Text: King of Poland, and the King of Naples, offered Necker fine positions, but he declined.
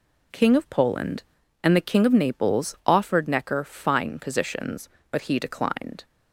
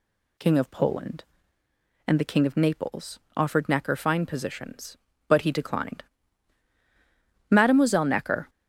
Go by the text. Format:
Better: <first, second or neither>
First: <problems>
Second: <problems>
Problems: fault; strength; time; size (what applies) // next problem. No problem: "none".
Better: first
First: none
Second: goes on to say "Mademoiselle Necker"; noticeable; from 7.4 s on; 1.0 s long